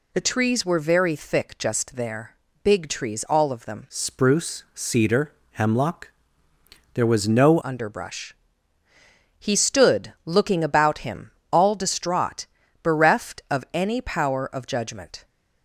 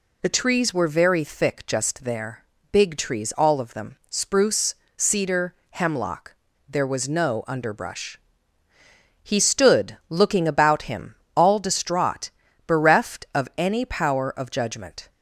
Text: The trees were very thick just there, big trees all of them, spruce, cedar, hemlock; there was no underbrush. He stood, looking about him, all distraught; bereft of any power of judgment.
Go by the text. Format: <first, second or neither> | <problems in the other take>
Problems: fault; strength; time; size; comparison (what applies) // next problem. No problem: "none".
second | changes voice from "spruce" to "no"; from 3.8 to 7.5 s; 3.7 s long